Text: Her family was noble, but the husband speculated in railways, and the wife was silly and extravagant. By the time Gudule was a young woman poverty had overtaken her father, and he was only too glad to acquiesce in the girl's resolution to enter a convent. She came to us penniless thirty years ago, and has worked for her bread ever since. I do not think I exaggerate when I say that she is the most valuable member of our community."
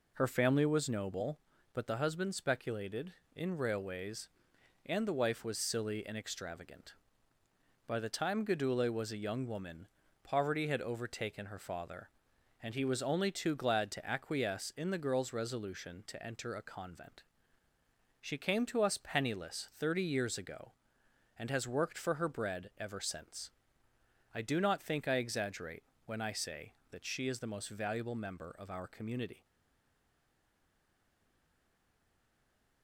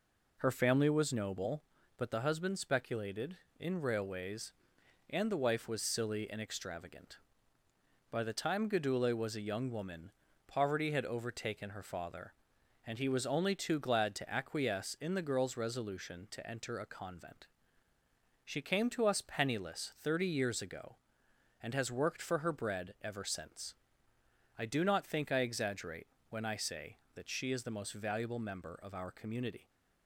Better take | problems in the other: second | pauses between "woman" and "poverty"; slight; at 9.8 s; 0.36 s long; slight in the second // pauses between "exaggerate" and "when"; slight; at 25.8 s; 0.24 s long; slight in the second // stays silent after the last word; strong; from 29.4 s on; 3.4 s long

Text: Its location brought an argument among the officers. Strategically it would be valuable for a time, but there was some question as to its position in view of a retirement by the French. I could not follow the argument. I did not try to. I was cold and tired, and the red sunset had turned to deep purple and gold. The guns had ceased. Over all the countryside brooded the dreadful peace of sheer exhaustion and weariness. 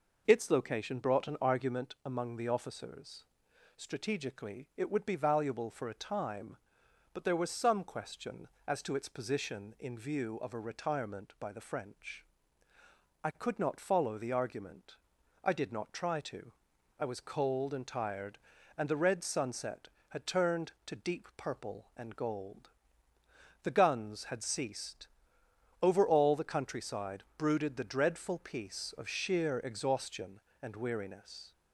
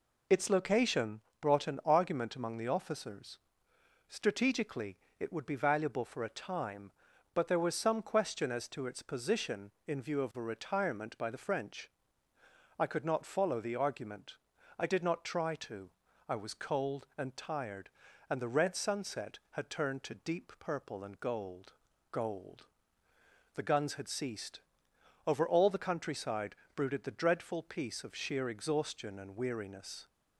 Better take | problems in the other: first | pauses between "location" and "brought"; slight; at 1.2 s; 0.22 s long // pauses between "Strategically" and "it"; slight; at 4.9 s; 0.22 s long // says "gold" twice; at 22.1 s // pauses between "countryside" and "brooded"; slight; at 26.5 s; 0.20 s long

